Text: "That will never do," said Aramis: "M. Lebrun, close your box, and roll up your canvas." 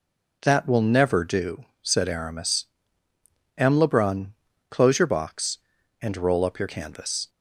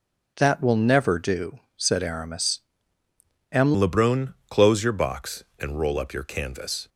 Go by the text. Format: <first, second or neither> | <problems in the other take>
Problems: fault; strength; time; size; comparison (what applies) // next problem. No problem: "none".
first | changes voice at "Lebrun"; from 3.7 s on; 3.1 s long